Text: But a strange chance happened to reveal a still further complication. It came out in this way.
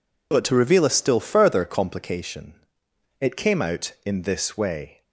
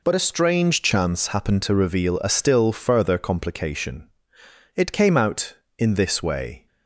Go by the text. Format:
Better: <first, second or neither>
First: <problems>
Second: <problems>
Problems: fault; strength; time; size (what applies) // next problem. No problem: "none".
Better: second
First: skips "a strange chance happened"; at 0.4 s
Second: none